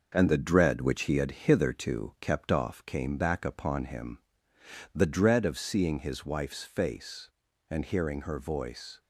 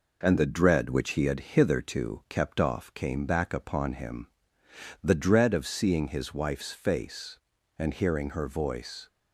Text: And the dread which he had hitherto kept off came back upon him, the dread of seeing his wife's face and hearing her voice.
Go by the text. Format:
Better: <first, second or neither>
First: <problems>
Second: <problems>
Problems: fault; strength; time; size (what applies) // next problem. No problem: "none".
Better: second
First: gets quieter; noticeable; throughout; 5 dB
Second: none